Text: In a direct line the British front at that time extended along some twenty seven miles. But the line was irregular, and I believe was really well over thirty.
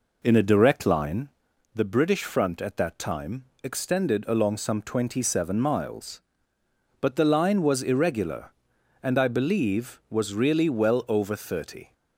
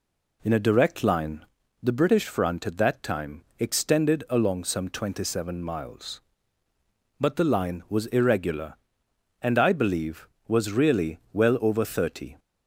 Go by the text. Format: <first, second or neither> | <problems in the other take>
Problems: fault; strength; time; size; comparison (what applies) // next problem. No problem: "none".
second | starts louder than the rest; noticeable; until 1.3 s; 4 dB // pauses between "line" and "the"; noticeable; at 1.2 s; 0.46 s long; also in the second // pauses between "time" and "extended"; slight; at 3.4 s; 0.18 s long; slight in the second